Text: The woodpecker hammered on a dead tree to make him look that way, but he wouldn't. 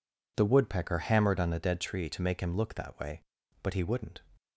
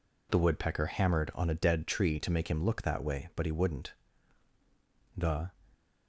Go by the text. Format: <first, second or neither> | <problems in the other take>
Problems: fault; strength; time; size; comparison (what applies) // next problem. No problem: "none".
first | goes on to say "The"; slight; from 5.1 s on; 0.34 s long